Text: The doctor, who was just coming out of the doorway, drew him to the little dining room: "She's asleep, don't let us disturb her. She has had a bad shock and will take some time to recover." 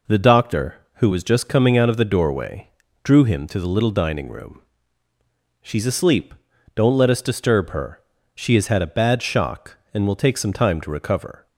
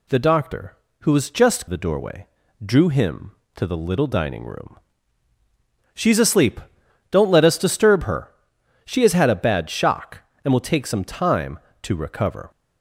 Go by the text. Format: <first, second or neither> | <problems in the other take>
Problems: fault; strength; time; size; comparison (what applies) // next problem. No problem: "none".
first | skips "coming out of"; at 1.6 s